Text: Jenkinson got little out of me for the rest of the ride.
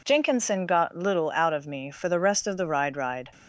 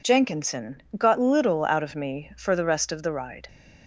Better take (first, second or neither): second